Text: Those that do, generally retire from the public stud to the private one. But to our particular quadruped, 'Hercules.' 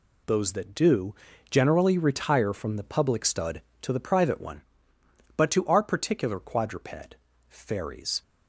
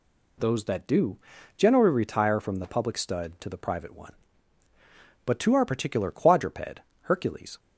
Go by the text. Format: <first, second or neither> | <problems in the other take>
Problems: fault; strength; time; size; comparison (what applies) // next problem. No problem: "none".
second | says "Fairies" for "Hercules"; at 7.4 s